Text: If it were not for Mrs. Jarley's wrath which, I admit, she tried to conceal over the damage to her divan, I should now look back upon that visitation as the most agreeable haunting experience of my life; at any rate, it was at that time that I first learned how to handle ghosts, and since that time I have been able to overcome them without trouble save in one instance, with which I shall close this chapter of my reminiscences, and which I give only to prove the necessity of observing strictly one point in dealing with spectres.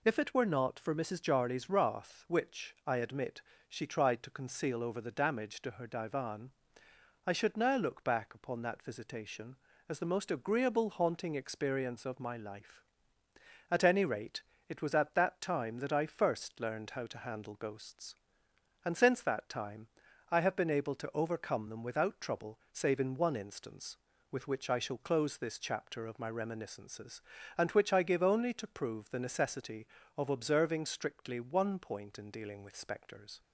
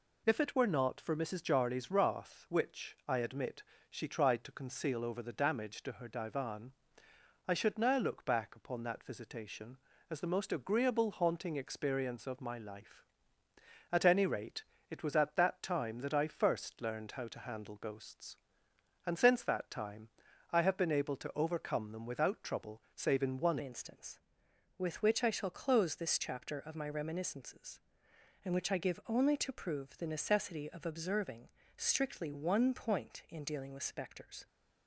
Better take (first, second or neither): first